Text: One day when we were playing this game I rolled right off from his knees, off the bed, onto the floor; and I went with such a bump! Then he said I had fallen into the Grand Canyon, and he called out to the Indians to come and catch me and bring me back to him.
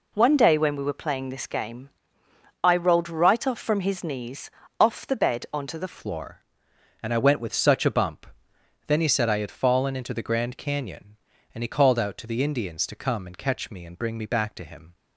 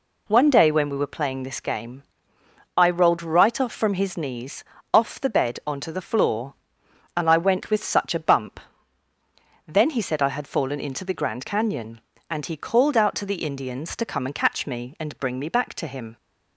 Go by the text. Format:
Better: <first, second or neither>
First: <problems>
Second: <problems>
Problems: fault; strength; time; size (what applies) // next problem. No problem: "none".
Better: second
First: pauses between "game" and "I"; noticeable; at 1.8 s; 0.72 s long // changes voice at "floor"; from 5.9 s on; 9.0 s long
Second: pauses between "game" and "I"; noticeable; at 2.0 s; 0.72 s long